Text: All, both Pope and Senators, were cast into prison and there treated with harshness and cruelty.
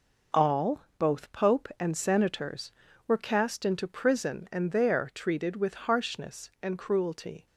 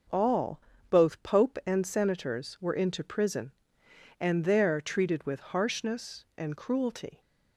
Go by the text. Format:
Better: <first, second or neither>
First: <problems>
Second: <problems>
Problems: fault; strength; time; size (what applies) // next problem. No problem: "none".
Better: first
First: none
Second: skips "cast"; at 2.7 s